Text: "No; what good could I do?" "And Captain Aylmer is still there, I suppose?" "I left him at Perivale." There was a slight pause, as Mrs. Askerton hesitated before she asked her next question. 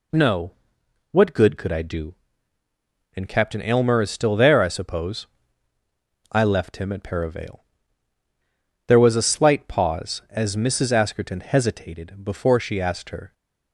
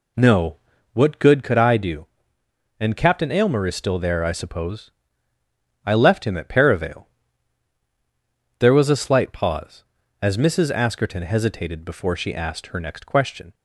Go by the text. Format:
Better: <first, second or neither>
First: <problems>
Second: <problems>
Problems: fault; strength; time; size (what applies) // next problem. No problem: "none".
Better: second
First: stops before "next question"; at 13.3 s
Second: none